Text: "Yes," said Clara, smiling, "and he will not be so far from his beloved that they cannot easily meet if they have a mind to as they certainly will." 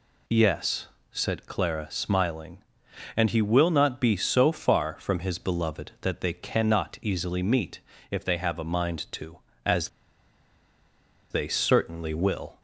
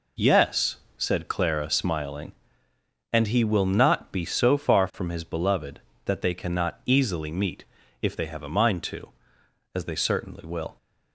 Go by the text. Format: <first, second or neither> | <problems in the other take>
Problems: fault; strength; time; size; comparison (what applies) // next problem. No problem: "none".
second | pauses between "meet" and "if"; slight; at 7.7 s; 0.32 s long; also in the second // pauses between "as" and "they"; strong; at 9.8 s; 1.4 s long